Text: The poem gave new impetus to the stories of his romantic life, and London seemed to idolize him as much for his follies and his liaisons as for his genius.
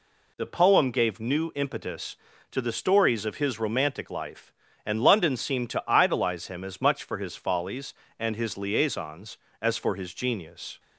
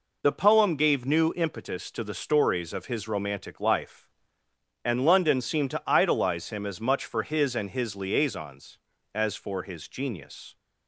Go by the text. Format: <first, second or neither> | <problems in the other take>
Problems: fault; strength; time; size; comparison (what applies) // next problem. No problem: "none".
first | skips "follies"; at 7.5 s